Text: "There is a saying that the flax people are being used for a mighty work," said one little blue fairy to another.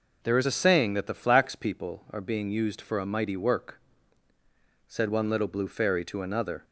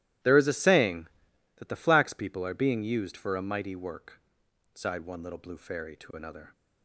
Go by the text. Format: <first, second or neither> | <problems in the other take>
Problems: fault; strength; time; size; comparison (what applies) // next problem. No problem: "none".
first | starts louder than the rest; strong; until 1.7 s; 14.5 dB // says "sighed" for "said"; at 4.7 s